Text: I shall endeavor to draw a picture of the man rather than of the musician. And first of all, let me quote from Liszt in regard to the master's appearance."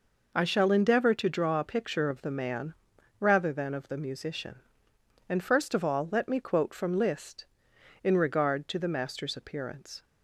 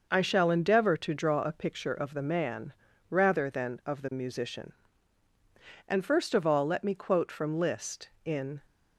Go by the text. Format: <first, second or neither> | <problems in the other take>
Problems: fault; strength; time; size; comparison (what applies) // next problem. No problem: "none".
first | pauses between "man" and "rather"; slight; at 2.7 s; 0.36 s long; noticeable in the first // stops before "regard to the master's appearance"; at 8.6 s